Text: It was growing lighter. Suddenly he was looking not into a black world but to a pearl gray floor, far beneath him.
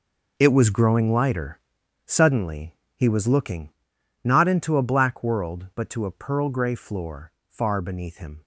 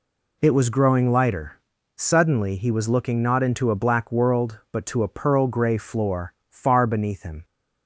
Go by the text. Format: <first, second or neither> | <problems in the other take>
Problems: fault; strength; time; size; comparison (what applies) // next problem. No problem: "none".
second | gets quieter; strong; throughout; 13 dB // pauses between "Suddenly" and "he"; slight; at 2.7 s; 0.20 s long // pauses between "looking" and "not"; noticeable; at 3.6 s; 0.54 s long